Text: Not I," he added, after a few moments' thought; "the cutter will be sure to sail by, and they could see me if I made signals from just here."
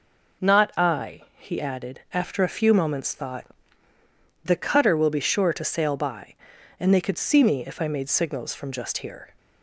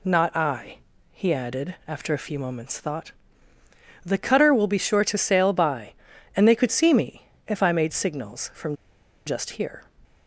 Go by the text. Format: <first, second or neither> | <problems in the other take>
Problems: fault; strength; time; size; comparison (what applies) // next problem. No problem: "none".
first | pauses between "me" and "if"; slight; at 7.2 s; 0.18 s long // pauses between "from" and "just"; noticeable; at 8.7 s; 0.51 s long